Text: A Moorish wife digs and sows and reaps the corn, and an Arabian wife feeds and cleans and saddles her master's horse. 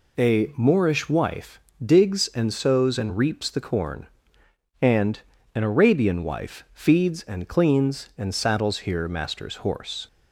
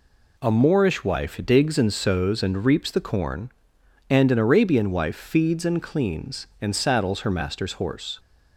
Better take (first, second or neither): second